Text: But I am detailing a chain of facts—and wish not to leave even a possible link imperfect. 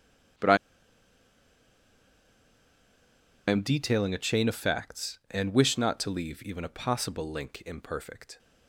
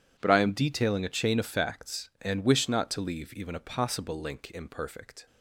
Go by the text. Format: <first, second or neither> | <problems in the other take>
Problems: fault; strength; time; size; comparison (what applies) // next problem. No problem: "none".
second | pauses between "I" and "am"; strong; at 0.5 s; 2.9 s long